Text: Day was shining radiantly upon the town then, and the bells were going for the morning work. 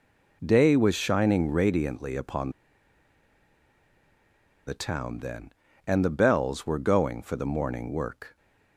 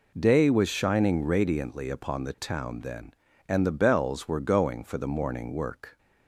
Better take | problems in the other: second | pauses between "upon" and "the"; strong; at 2.5 s; 2.1 s long

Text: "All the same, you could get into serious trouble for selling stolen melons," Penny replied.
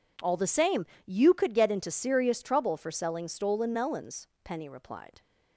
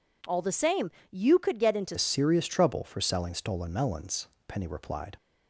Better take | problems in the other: first | changes voice at "serious"; from 1.9 s on; 3.2 s long

